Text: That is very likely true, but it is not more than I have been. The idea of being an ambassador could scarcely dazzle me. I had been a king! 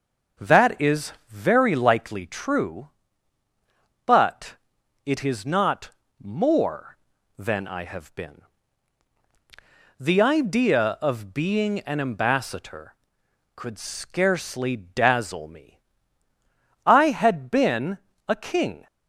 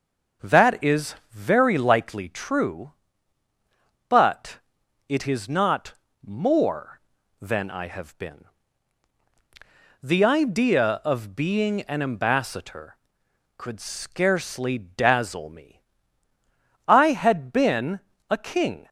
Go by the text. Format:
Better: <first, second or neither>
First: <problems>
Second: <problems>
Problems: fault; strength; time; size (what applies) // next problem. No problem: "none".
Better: neither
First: pauses between "is" and "very"; slight; at 1.1 s; 0.16 s long // pauses between "but" and "it"; noticeable; at 4.5 s; 0.48 s long // pauses between "not" and "more"; slight; at 5.9 s; 0.32 s long // pauses between "been" and "a"; slight; at 17.9 s; 0.32 s long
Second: pauses between "is" and "very"; slight; at 1.1 s; 0.16 s long // pauses between "but" and "it"; noticeable; at 4.5 s; 0.48 s long // pauses between "not" and "more"; slight; at 5.9 s; 0.32 s long // pauses between "been" and "a"; slight; at 17.9 s; 0.32 s long